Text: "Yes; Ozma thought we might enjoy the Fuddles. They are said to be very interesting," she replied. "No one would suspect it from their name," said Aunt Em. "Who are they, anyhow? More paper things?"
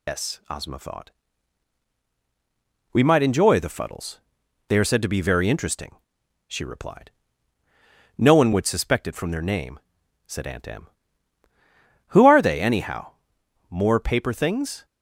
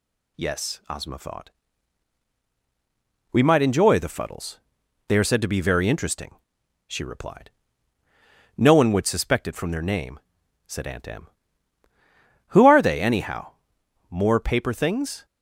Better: second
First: loses the start of "Yes"; at 0.0 s; 115 ms // pauses between "thought" and "we"; strong; at 1.0 s; 1.8 s long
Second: pauses between "thought" and "we"; strong; at 1.4 s; 1.8 s long

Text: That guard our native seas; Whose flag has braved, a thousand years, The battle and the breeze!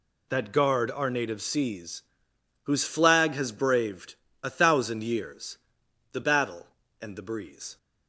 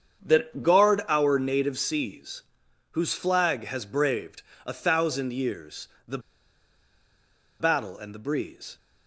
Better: first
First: none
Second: starts louder than the rest; strong; until 1.3 s; 7.5 dB // pauses between "The" and "battle"; strong; at 6.1 s; 1.4 s long

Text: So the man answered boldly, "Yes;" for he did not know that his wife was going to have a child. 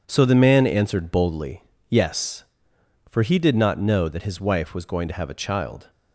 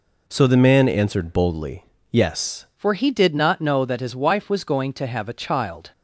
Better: first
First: none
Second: changes voice at "for"; from 2.7 s on; 3.2 s long

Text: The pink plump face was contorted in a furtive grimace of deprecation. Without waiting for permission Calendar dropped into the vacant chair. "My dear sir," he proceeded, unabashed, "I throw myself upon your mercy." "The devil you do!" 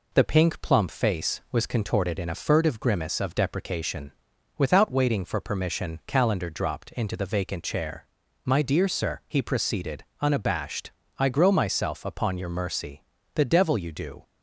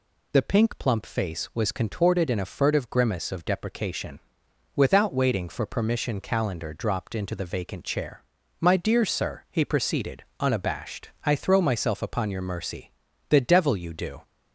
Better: second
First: says "grow" for "throw"; at 11.2 s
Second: none

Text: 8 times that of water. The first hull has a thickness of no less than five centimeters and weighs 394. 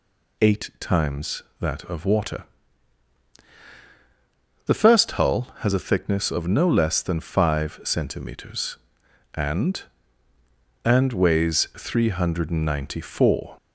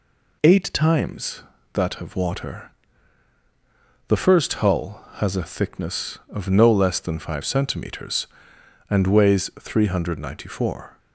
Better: second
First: says "and" twice; at 10.8 s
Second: none

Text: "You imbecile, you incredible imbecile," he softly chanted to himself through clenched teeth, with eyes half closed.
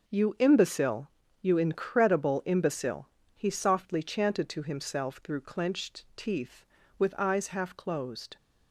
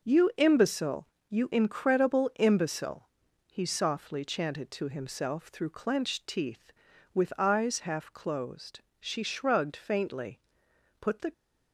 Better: first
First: none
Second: goes on to say "She shrugged faintly put the"; strong; from 8.9 s on; 2.3 s long

